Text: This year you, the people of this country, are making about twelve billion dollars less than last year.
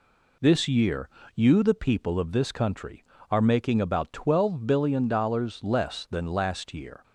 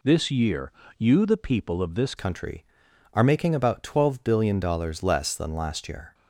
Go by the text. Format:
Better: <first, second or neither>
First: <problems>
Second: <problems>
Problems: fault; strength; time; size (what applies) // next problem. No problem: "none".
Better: first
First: pauses between "year" and "you"; slight; at 1.0 s; 0.26 s long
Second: pauses between "year" and "you"; slight; at 0.7 s; 0.26 s long // changes voice at "country"; from 2.1 s on; 4.0 s long